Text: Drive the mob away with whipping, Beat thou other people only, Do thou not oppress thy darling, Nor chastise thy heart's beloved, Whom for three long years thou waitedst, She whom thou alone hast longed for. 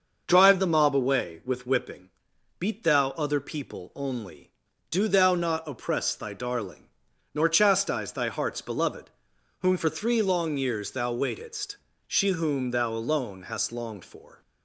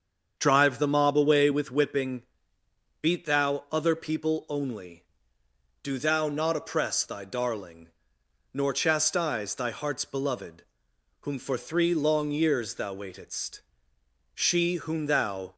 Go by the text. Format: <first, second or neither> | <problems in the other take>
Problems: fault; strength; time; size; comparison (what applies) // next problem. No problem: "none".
first | starts louder than the rest; strong; until 1.3 s; 7 dB; also in the first // stops before "alone hast longed for"; at 15.5 s